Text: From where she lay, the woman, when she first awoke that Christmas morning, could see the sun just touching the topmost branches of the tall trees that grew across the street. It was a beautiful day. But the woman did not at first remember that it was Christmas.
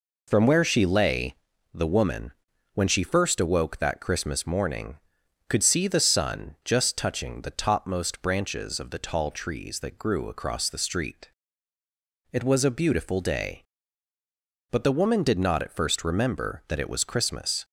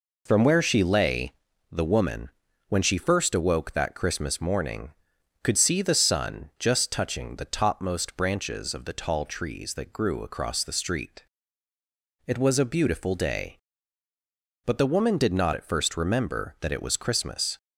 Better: neither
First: none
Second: none

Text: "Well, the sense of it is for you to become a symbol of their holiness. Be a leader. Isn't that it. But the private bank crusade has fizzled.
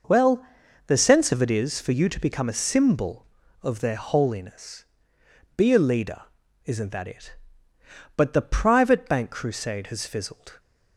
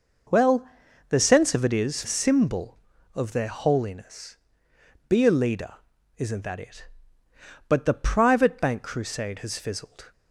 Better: first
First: none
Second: skips "for you to become"; at 2.0 s

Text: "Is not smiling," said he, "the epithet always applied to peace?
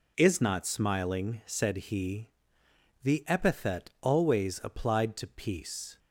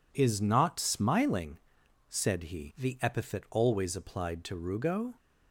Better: first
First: none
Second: says "rugo" for "peace"; at 4.5 s

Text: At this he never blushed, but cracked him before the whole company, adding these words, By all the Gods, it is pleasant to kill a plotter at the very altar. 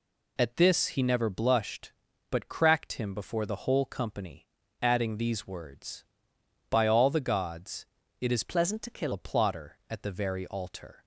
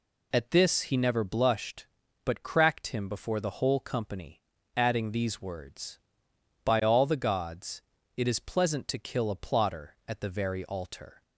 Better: second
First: changes voice from "pleasant" to "kill"; from 8.4 to 9.1 s; 0.7 s long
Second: none

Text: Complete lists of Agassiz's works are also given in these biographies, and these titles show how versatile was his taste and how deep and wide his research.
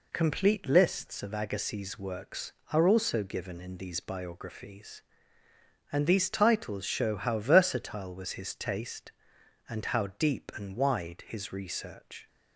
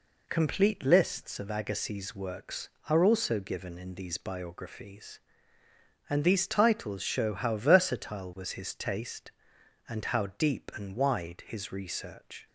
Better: neither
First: none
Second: none

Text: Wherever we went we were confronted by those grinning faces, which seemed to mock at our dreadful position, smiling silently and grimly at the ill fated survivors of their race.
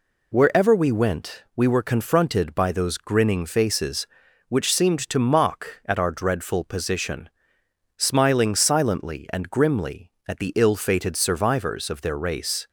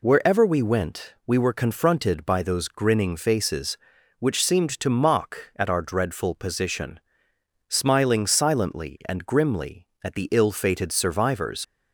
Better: first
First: none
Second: stops before "of their race"; at 11.6 s

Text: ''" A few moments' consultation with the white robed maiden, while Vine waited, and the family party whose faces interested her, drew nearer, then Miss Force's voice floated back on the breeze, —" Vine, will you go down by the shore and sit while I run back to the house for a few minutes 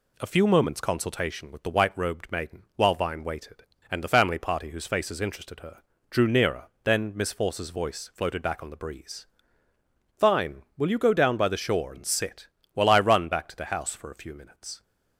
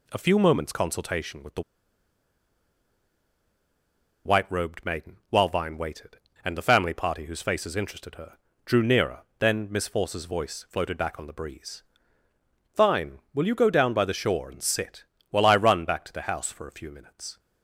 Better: first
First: pauses between "sit" and "while"; slight; at 12.4 s; 0.26 s long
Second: pauses between "the" and "white"; strong; at 1.6 s; 2.6 s long // pauses between "sit" and "while"; slight; at 15.0 s; 0.26 s long

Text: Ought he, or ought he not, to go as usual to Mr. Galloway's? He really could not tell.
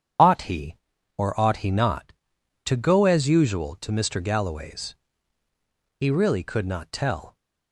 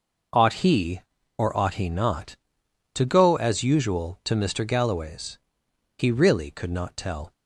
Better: second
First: loses the start of "Ought"; at 0.1 s; 30 ms // starts louder than the rest; strong; until 1.6 s; 8.5 dB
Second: none

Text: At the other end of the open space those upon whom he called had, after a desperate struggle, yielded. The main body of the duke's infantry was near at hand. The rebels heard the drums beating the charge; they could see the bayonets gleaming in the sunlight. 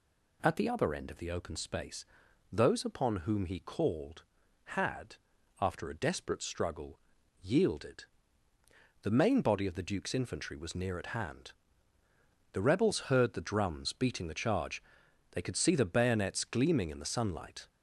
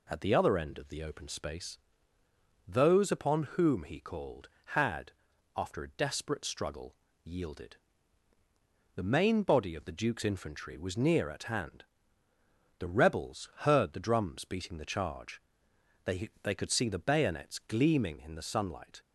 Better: first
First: pauses between "space" and "those"; noticeable; at 2.0 s; 0.48 s long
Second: pauses between "space" and "those"; noticeable; at 1.7 s; 0.92 s long // says "they" twice; at 16.4 s

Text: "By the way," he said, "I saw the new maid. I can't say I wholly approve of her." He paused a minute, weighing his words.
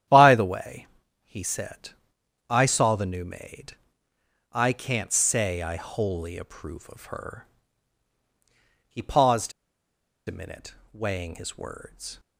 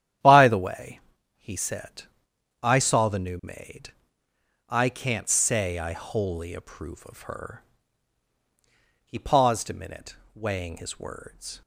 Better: second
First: starts louder than the rest; strong; until 1.4 s; 10.5 dB // pauses between "paused" and "a"; noticeable; at 9.5 s; 0.75 s long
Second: starts louder than the rest; strong; until 1.6 s; 10.5 dB

